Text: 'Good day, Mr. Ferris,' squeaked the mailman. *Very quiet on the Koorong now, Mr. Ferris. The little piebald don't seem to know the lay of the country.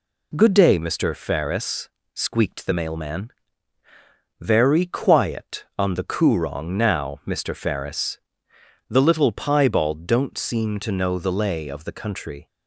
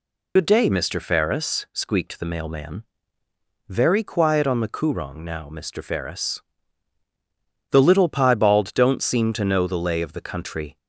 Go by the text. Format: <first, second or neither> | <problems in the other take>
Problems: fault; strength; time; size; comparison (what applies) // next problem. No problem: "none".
first | loses the start of "Good"; at 0.3 s; 35 ms